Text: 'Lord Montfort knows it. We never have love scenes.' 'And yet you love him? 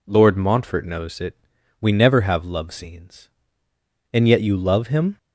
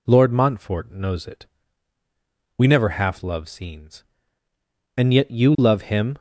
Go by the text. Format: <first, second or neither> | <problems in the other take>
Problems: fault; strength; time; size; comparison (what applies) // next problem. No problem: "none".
first | says "half" for "have"; at 2.8 s